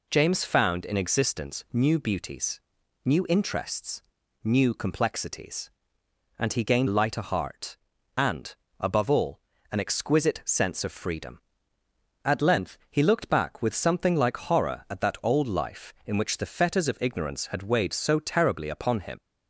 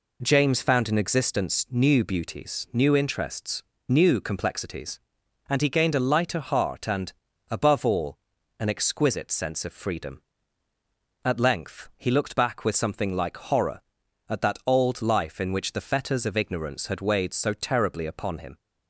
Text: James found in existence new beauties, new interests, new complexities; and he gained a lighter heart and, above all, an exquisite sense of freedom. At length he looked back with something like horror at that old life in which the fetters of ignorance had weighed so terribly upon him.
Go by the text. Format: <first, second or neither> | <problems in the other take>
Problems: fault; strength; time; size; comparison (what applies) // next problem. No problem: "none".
second | skips "a"; at 6.8 s